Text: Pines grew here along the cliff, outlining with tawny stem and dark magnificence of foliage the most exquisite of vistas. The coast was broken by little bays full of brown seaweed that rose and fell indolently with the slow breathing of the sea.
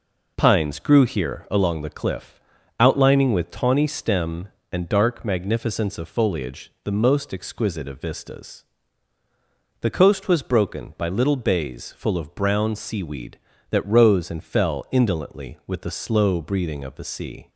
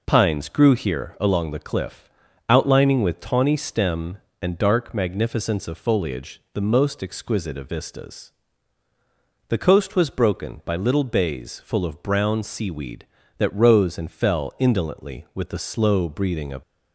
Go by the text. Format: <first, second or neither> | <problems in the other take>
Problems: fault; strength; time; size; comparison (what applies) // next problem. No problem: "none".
first | stops before "the sea"; at 16.6 s